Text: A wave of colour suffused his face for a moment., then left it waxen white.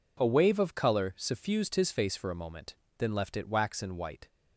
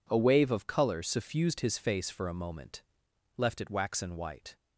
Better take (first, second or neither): first